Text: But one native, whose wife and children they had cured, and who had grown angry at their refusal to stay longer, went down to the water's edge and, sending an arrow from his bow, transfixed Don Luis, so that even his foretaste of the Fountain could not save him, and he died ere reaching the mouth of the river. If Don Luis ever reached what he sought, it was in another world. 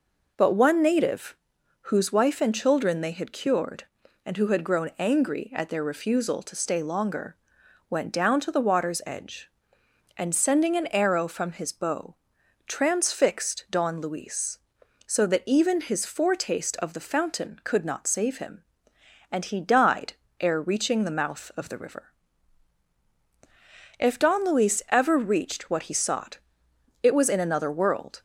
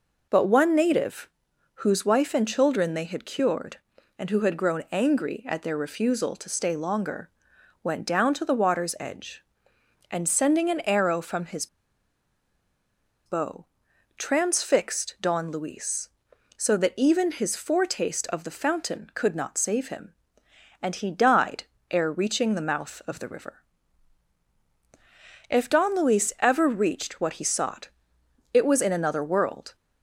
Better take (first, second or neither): first